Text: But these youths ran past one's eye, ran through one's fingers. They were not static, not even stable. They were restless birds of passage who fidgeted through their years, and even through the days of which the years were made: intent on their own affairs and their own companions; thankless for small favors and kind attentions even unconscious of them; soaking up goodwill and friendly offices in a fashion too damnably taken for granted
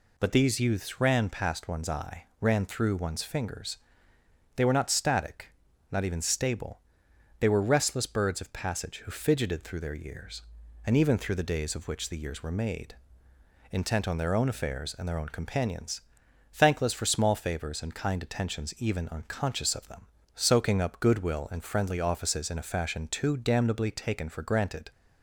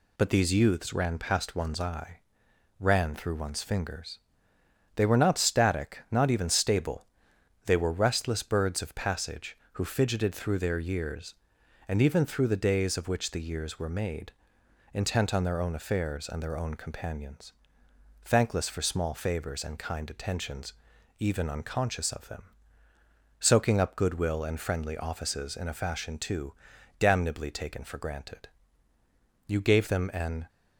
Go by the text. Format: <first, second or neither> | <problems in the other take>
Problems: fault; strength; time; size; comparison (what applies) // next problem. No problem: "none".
first | pauses between "attentions" and "even"; noticeable; at 20.7 s; 0.48 s long // pauses between "too" and "damnably"; at 26.5 s; 0.44 s long // goes on to say "You gave them an"; noticeable; from 29.4 s on; 0.98 s long